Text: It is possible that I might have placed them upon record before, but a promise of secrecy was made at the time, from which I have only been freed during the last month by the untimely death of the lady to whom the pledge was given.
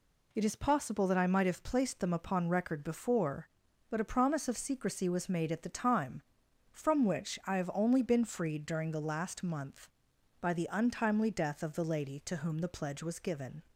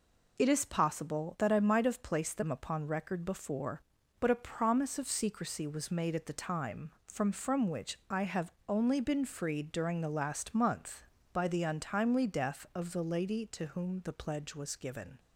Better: first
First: none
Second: says "from" twice; at 7.3 s // pauses between "have" and "only"; slight; at 8.5 s; 0.16 s long

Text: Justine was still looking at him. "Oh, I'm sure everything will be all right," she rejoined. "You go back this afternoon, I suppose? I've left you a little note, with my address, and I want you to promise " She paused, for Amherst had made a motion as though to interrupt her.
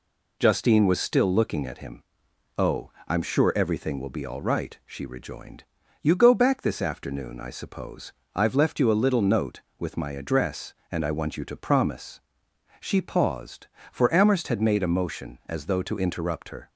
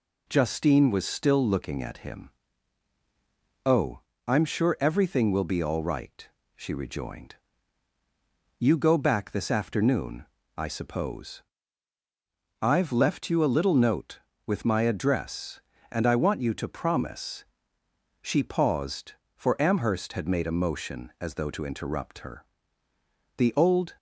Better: first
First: none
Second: goes on to say "The old"; from 23.3 s on; 0.60 s long

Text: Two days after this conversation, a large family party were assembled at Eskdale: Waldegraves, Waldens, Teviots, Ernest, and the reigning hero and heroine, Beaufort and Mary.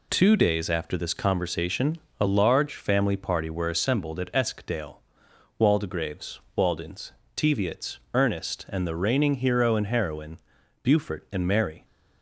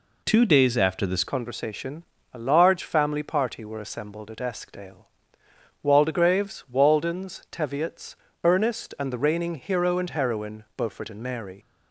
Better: first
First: none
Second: changes voice at "conversation"; from 1.2 s on; 10.3 s long

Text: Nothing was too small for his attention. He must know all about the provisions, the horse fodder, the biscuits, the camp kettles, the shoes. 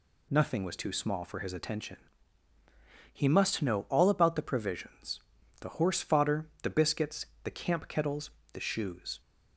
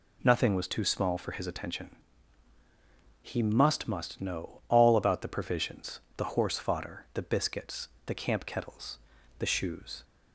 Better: first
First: none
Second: says "must" twice; at 3.8 s

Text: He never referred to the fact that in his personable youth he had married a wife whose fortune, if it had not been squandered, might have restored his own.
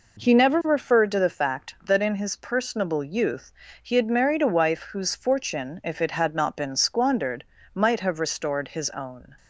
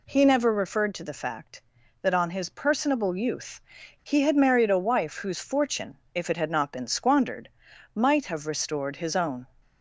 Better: first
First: pauses between "youth" and "he"; slight; at 3.5 s; 0.32 s long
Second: says "on" for "in"; at 2.1 s // pauses between "youth" and "he"; at 3.6 s; 0.42 s long

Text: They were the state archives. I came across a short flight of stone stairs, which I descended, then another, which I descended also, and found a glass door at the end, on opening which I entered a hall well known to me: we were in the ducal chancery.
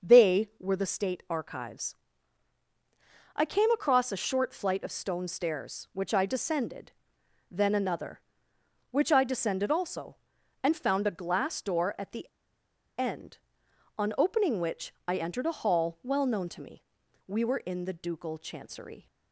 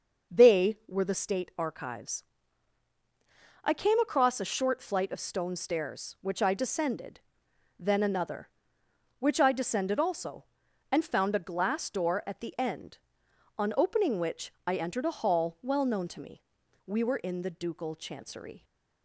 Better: second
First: pauses between "the" and "end"; noticeable; at 12.2 s; 0.72 s long // pauses between "which" and "I"; slight; at 14.9 s; 0.16 s long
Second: pauses between "which" and "I"; slight; at 14.5 s; 0.16 s long

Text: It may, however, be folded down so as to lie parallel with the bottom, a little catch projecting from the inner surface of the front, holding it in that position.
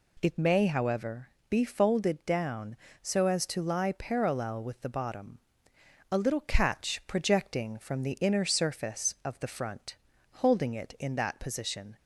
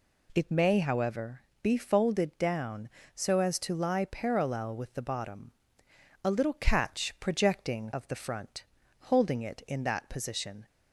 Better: first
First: none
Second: skips "from the inner surface"; at 7.9 s

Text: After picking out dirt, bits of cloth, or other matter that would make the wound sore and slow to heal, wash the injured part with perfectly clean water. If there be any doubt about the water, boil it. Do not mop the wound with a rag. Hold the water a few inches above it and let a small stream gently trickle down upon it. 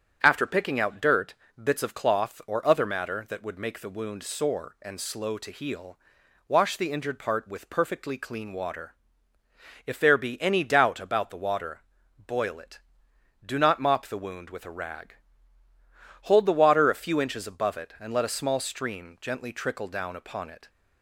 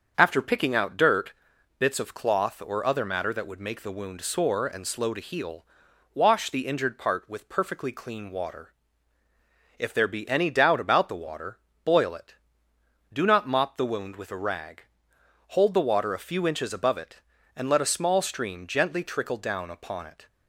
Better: neither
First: starts louder than the rest; strong; until 1.2 s; 7 dB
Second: starts louder than the rest; until 1.1 s; 7 dB

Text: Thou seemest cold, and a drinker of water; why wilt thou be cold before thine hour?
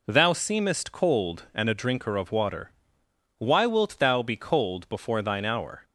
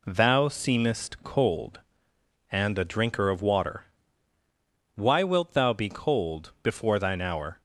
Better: neither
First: none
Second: none

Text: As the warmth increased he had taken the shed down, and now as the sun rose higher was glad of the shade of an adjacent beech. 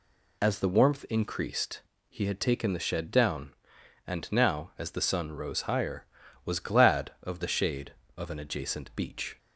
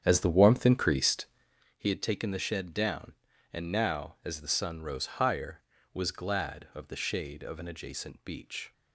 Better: first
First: pauses between "increased" and "he"; slight; at 1.8 s; 0.28 s long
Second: starts louder than the rest; strong; until 1.7 s; 9 dB // pauses between "increased" and "he"; noticeable; at 1.2 s; 0.50 s long

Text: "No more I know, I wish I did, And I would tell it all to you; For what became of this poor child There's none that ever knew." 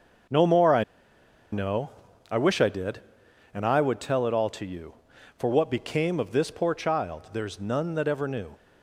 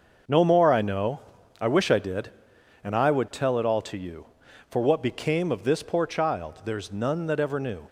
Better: second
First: starts louder than the rest; noticeable; until 2.4 s; 6 dB // pauses between "I" and "know"; noticeable; at 0.8 s; 0.70 s long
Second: starts louder than the rest; until 1.6 s; 6 dB

